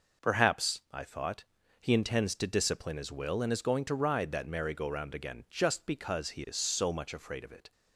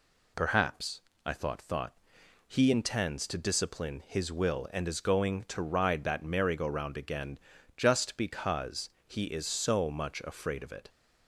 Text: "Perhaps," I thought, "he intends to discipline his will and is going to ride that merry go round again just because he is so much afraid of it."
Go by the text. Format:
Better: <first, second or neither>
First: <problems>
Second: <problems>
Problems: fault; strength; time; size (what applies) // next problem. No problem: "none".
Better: first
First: none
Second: says "thought" twice; at 1.6 s // pauses between "again" and "just"; at 7.3 s; 0.40 s long // pauses between "because" and "he"; slight; at 8.8 s; 0.18 s long